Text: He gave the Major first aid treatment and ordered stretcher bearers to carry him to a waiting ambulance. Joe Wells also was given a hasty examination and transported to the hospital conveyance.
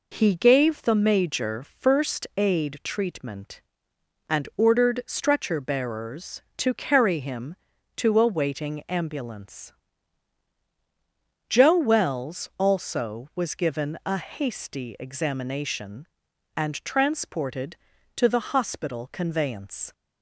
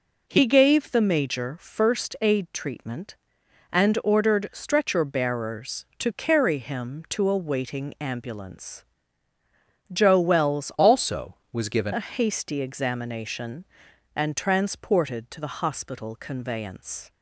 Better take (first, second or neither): first